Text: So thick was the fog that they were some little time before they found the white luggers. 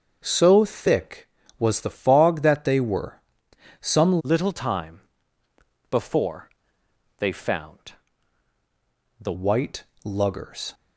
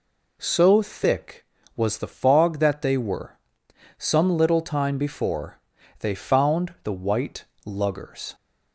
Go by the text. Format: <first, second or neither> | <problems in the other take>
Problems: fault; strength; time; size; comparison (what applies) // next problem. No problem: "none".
second | starts louder than the rest; noticeable; until 1.2 s; 6 dB // pauses between "were" and "some"; noticeable; at 3.2 s; 0.60 s long; noticeable in the second // changes voice from "little" to "the"; from 4.2 to 9.3 s; 5.1 s long // pauses between "time" and "before"; noticeable; at 5.0 s; 0.88 s long // pauses between "before" and "they"; noticeable; at 6.5 s; 0.66 s long; also in the second // pauses between "found" and "the"; strong; at 7.9 s; 1.2 s long // pauses between "white" and "luggers"; slight; at 9.8 s; 0.20 s long; slight in the second